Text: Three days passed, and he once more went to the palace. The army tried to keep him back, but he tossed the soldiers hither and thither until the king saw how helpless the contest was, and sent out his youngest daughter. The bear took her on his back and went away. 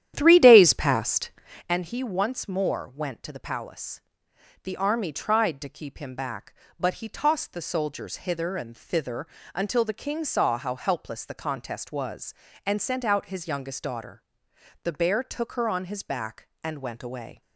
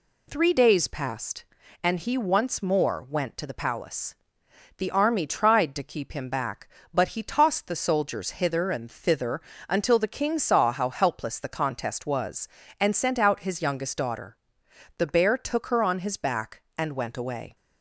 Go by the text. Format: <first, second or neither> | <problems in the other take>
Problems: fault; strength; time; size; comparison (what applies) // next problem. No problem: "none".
second | starts louder than the rest; strong; until 1.8 s; 11 dB // pauses between "thither" and "until"; slight; at 9.2 s; 0.28 s long; slight in the second